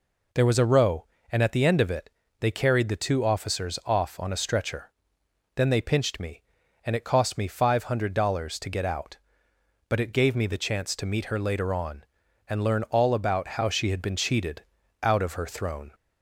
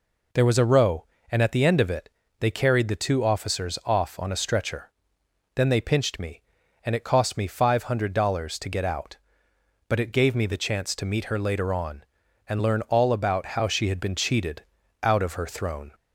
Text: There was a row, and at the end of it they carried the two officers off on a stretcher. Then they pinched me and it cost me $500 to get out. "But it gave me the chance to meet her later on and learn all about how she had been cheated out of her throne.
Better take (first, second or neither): neither